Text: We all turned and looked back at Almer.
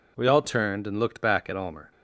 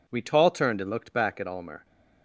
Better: first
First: none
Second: says "tall" for "all"; at 0.2 s

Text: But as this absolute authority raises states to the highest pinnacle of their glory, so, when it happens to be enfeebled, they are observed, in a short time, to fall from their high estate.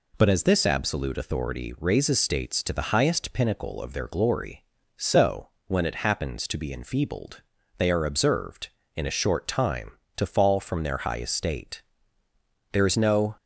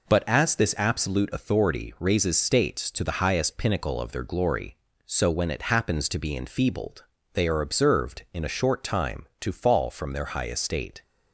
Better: second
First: goes on to say "There is no"; noticeable; from 12.7 s on; 0.64 s long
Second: none

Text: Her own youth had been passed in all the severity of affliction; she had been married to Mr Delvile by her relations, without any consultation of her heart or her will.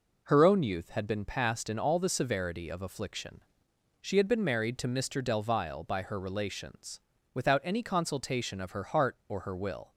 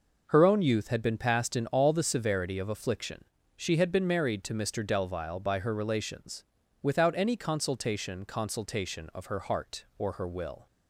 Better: first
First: none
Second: says "consultation" twice; at 8.2 s

